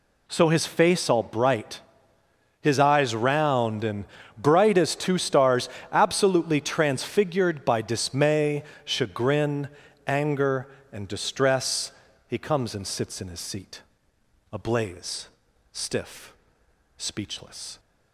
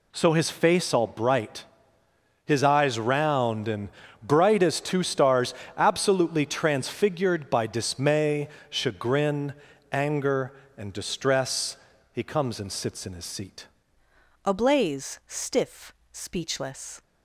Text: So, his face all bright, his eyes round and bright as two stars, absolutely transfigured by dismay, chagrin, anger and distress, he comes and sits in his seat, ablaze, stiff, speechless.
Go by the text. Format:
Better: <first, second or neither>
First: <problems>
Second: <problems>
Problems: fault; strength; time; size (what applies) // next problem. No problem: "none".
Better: first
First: pauses between "and" and "bright"; slight; at 4.0 s; 0.33 s long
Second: pauses between "and" and "bright"; slight; at 3.8 s; 0.34 s long // changes voice at "ablaze"; from 14.4 s on; 2.6 s long